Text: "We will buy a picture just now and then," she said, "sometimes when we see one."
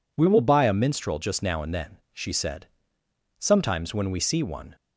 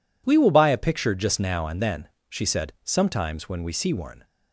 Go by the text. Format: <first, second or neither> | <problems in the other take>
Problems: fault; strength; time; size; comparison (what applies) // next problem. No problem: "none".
second | says "minstrel" for "picture"; at 0.7 s